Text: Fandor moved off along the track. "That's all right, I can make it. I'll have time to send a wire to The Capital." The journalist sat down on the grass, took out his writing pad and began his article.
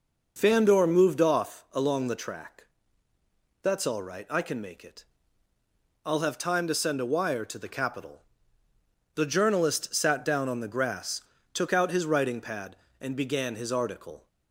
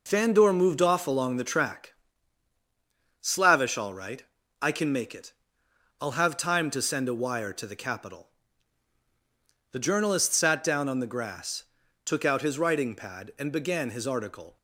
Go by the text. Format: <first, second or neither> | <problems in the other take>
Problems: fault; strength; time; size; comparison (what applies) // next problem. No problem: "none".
first | says "Slavish" for "That's"; at 3.1 s